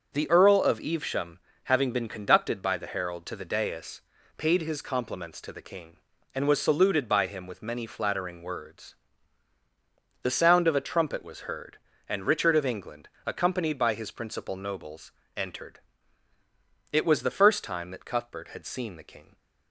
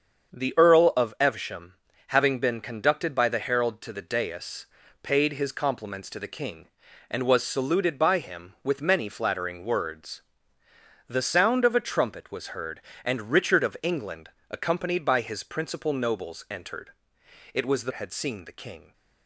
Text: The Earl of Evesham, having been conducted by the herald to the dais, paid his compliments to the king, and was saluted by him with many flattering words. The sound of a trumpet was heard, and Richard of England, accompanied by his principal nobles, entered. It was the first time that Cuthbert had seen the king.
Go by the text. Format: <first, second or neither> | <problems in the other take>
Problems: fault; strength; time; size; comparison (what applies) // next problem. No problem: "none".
first | starts louder than the rest; until 1.4 s; 7 dB; also in the first // skips "first time that Cuthbert"; at 17.9 s